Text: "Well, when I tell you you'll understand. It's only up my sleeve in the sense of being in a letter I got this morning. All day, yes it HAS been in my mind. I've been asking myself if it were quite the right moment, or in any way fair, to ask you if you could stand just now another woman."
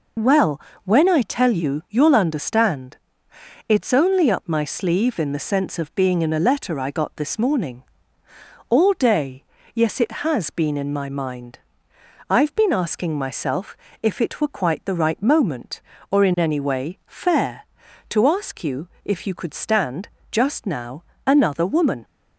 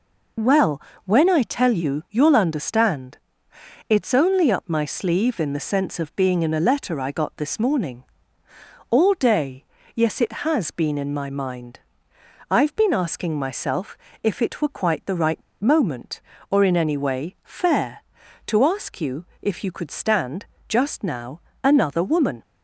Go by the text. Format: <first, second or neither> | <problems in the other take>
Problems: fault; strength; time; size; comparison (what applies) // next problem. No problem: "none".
first | pauses between "myself" and "if"; slight; at 13.9 s; 0.26 s long; slight in the first // pauses between "right" and "moment"; slight; at 15.4 s; 0.20 s long // pauses between "you" and "if"; slight; at 19.2 s; 0.16 s long; slight in the first // pauses between "stand" and "just"; slight; at 20.4 s; 0.22 s long; slight in the first // pauses between "now" and "another"; slight; at 21.3 s; 0.22 s long; slight in the first